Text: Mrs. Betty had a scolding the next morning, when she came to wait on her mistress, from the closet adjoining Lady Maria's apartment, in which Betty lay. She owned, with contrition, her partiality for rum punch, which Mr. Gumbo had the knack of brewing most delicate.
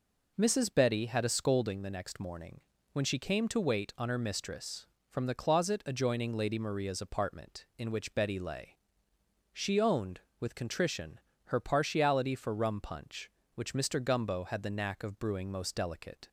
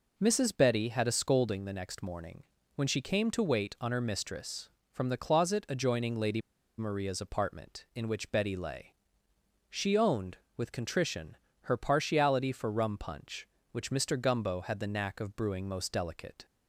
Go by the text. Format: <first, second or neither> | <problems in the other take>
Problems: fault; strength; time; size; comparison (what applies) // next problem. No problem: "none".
first | pauses between "Lady" and "Maria's"; at 6.4 s; 0.37 s long